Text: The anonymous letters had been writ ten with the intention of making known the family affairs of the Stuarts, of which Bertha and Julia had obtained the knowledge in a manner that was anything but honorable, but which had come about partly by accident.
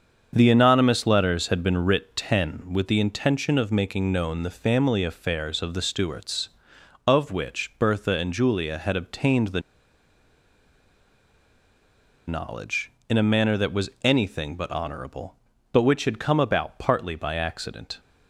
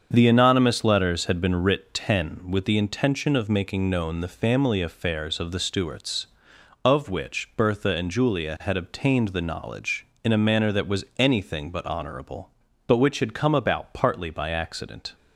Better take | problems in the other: second | starts louder than the rest; until 1.3 s; 7 dB; also in the second // pauses between "the" and "knowledge"; strong; at 9.5 s; 2.6 s long

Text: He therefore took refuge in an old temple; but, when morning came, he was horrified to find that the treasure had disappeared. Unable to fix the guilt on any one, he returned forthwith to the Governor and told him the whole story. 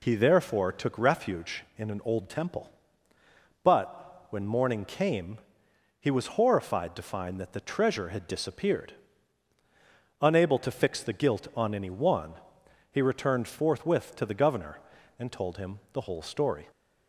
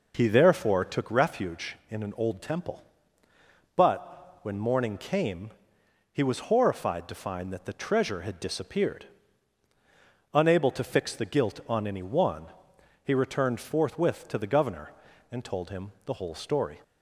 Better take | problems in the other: first | starts louder than the rest; noticeable; until 1.0 s; 4.5 dB

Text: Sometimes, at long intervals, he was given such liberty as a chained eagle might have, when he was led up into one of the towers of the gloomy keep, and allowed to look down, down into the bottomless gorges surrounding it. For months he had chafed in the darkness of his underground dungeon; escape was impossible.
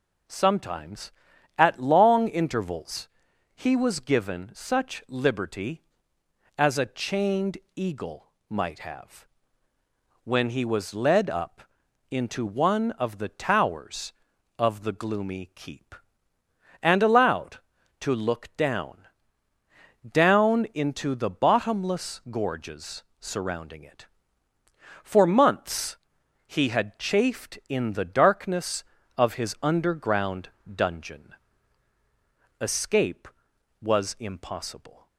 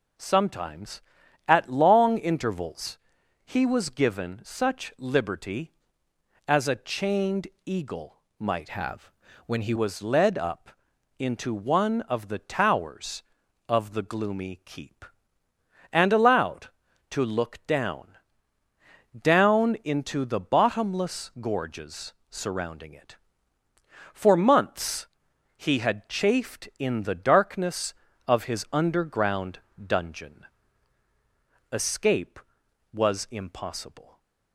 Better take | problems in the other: first | pauses between "chained" and "eagle"; slight; at 7.4 s; 0.18 s long; slight in the first // pauses between "eagle" and "might"; slight; at 8.1 s; 0.20 s long; slight in the first // changes voice from "have" to "he"; from 8.6 to 9.7 s; 1.1 s long // pauses between "up" and "into"; noticeable; at 10.7 s; 0.48 s long; noticeable in the first // pauses between "gorges" and "surrounding"; slight; at 22.1 s; 0.18 s long; slight in the first // pauses between "months" and "he"; noticeable; at 25.0 s; 0.50 s long; noticeable in the first // pauses between "underground" and "dungeon"; slight; at 29.5 s; 0.26 s long; slight in the first

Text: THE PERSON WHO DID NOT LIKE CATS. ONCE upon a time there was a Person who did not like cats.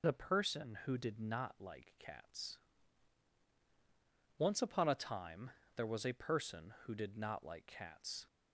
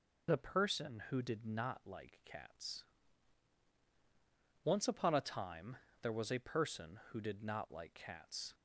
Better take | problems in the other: neither | pauses between "time" and "there"; slight; the same in both

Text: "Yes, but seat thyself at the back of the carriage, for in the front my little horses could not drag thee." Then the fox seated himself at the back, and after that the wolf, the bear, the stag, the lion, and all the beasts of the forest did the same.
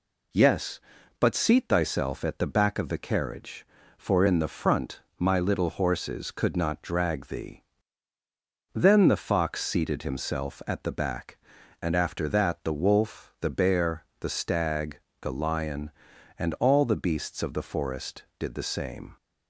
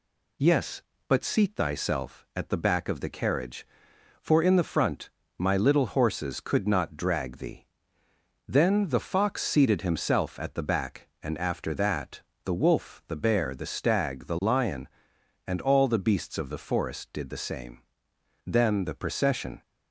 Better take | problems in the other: first | pauses between "front" and "my"; slight; at 5.0 s; 0.28 s long; slight in the first // pauses between "that" and "the"; slight; at 12.2 s; 0.24 s long // goes on to say "Then the procession"; noticeable; from 18.4 s on; 1.1 s long

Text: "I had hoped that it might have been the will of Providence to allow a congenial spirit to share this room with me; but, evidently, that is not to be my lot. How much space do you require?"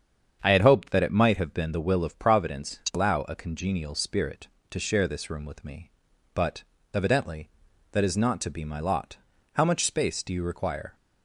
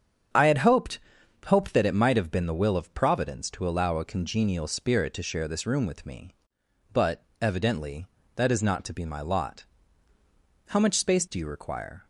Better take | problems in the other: first | starts louder than the rest; strong; until 1.8 s; 8 dB; strong in the first // says "hoped" twice; at 1.4 s

